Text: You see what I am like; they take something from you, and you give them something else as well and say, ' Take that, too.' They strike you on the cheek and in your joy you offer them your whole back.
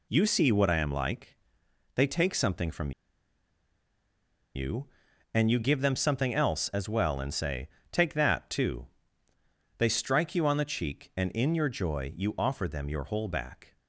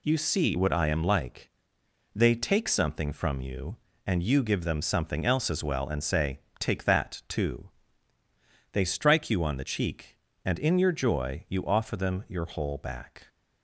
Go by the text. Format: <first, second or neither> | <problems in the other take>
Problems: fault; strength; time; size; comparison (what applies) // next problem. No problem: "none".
second | pauses between "from" and "you"; strong; at 2.9 s; 1.6 s long